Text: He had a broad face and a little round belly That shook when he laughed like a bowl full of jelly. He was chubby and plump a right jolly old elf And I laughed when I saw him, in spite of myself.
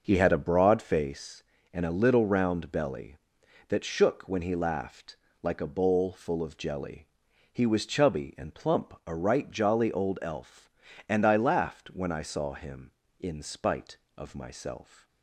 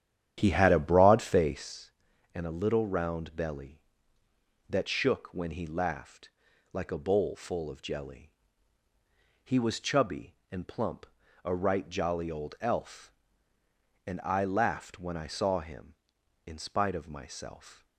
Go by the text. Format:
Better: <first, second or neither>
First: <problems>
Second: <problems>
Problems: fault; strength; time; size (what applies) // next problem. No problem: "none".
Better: first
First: pauses between "laughed" and "like"; slight; at 5.1 s; 0.26 s long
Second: starts louder than the rest; strong; until 1.8 s; 10 dB // pauses between "laughed" and "like"; at 6.2 s; 0.42 s long // pauses between "plump" and "a"; at 11.0 s; 0.38 s long